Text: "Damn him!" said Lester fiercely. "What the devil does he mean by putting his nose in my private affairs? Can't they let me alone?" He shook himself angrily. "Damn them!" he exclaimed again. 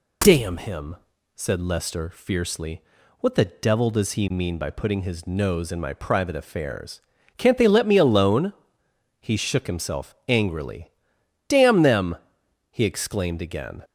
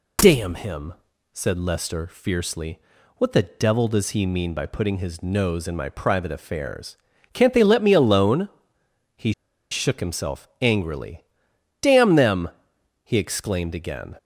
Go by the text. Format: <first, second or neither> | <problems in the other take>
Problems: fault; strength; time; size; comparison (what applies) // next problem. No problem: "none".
first | pauses between "He" and "shook"; at 9.3 s; 0.39 s long